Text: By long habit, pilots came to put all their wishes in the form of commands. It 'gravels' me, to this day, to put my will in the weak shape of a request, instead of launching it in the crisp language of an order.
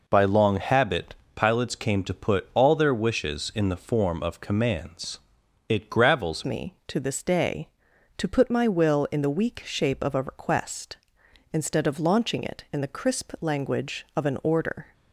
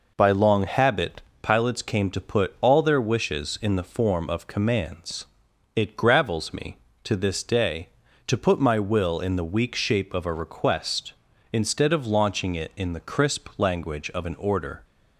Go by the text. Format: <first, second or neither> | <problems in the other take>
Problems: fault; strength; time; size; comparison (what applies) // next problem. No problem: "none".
second | changes voice at "me"; from 6.4 s on; 8.5 s long